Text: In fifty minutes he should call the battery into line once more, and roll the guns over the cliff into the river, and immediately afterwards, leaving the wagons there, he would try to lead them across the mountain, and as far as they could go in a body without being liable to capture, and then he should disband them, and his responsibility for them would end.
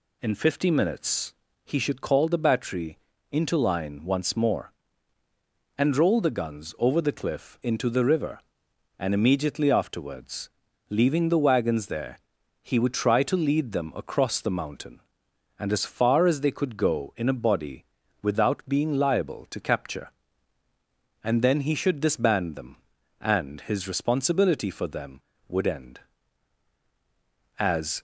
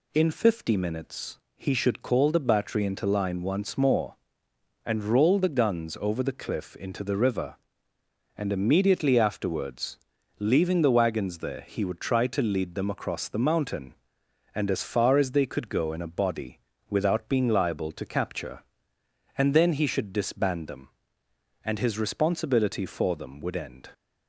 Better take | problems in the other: second | pauses between "minutes" and "he"; slight; at 1.3 s; 0.30 s long; slight in the second // pauses between "battery" and "into"; slight; at 2.9 s; 0.34 s long // pauses between "body" and "without"; at 17.8 s; 0.40 s long; slight in the second // goes on to say "As"; slight; from 27.5 s on; 0.42 s long

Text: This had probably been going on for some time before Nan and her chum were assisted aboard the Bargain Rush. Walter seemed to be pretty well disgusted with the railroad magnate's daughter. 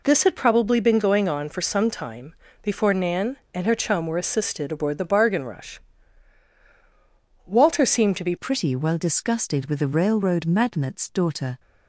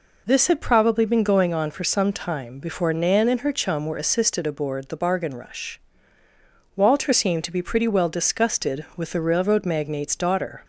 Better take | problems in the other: second | pauses between "time" and "before"; slight; at 2.3 s; 0.26 s long // changes voice at "pretty"; from 8.3 s on; 3.2 s long

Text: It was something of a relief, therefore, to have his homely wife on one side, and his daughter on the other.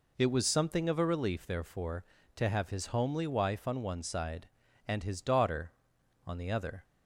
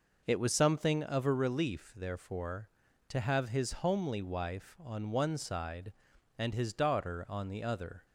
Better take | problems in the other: neither | none

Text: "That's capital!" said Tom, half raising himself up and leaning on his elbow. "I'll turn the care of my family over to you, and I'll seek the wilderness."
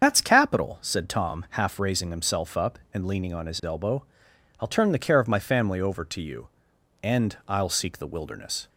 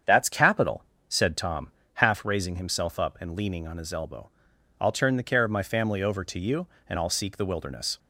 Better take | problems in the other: second | loses the start of "That's"; at 0.0 s; 125 ms // starts louder than the rest; strong; until 1.0 s; 7 dB; strong in the second

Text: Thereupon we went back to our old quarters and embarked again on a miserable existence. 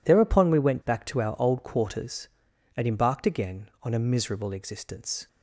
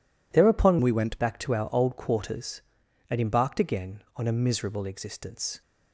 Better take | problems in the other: first | changes voice from "we" to "went"; from 0.8 to 1.2 s; 0.4 s long

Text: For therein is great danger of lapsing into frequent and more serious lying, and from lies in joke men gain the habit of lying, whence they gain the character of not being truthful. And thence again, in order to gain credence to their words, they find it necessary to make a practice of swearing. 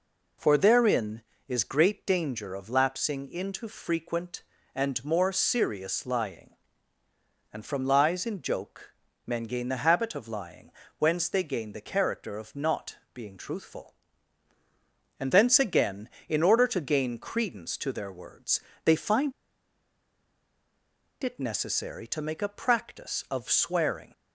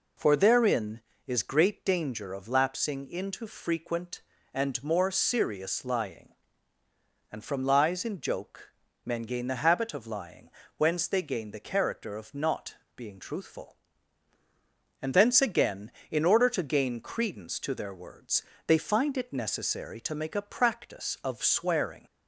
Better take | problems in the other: second | pauses between "joke" and "men"; slight; at 8.9 s; 0.34 s long; slight in the second // pauses between "not" and "being"; slight; at 12.9 s; 0.18 s long; slight in the second // pauses between "find" and "it"; strong; at 19.3 s; 1.9 s long

